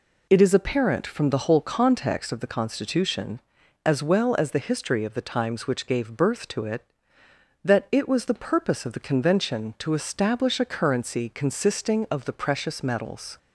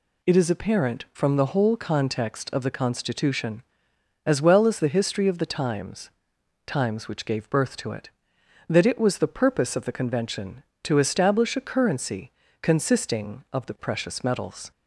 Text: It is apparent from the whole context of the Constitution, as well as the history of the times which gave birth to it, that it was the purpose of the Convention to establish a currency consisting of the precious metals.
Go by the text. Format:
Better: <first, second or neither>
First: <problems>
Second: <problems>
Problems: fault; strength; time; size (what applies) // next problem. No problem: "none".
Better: first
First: none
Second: says "times" twice; at 6.6 s // pauses between "currency" and "consisting"; slight; at 12.3 s; 0.32 s long